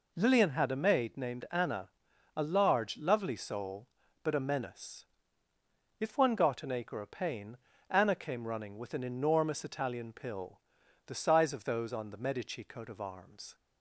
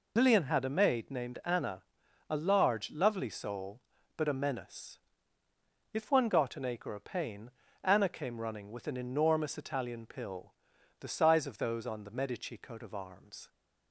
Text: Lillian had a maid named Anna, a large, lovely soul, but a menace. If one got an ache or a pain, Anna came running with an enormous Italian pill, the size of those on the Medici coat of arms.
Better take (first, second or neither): first